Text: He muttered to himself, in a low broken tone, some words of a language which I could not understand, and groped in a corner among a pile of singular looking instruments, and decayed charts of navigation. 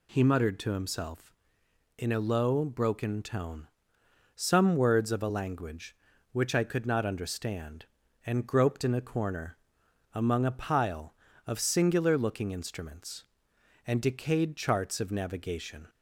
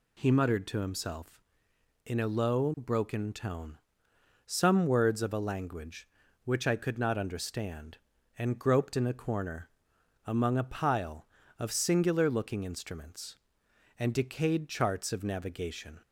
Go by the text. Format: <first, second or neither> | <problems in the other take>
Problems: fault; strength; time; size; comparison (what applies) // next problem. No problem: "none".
neither | pauses between "corner" and "among"; noticeable; the same in both